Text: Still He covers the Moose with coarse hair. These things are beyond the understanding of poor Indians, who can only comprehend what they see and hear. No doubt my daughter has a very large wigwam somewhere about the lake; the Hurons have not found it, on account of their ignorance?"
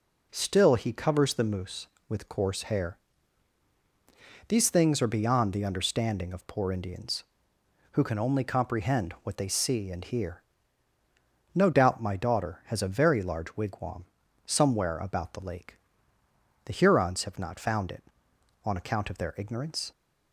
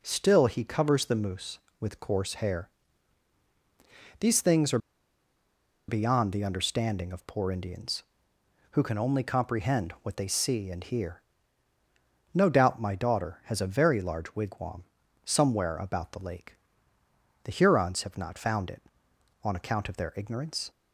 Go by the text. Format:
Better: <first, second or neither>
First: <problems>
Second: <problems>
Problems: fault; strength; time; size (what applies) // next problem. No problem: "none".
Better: first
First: pauses between "wigwam" and "somewhere"; at 14.0 s; 0.40 s long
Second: pauses between "are" and "beyond"; at 4.7 s; 1.1 s long // pauses between "wigwam" and "somewhere"; at 14.8 s; 0.40 s long